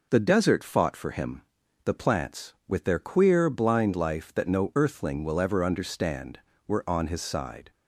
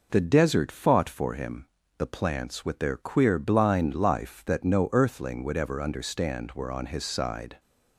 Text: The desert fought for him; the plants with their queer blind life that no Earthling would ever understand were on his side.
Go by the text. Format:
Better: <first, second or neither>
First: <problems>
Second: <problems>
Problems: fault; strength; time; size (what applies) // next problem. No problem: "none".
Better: second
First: says "will" for "would"; at 5.2 s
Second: none